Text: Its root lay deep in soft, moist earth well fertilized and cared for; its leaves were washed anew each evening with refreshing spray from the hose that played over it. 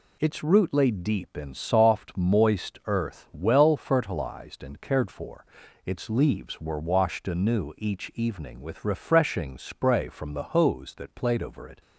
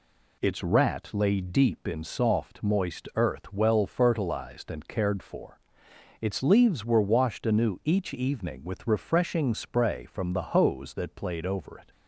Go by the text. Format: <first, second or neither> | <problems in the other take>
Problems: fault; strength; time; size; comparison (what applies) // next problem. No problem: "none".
first | says "rat" for "root"; at 0.6 s